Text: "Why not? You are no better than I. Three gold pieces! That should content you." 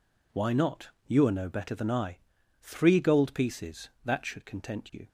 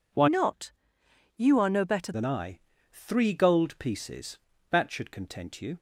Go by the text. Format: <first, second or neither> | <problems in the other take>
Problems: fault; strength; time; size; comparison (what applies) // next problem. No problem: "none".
first | changes voice from "not" to "better"; from 0.2 to 2.1 s; 1.9 s long